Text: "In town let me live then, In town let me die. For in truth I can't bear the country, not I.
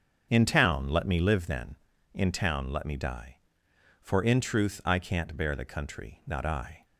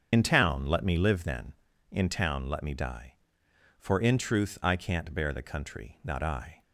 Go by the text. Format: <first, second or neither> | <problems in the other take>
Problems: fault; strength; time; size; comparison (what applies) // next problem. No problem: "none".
first | loses the start of "In"; at 0.1 s; 50 ms // starts louder than the rest; strong; until 1.1 s; 7.5 dB; strong in the first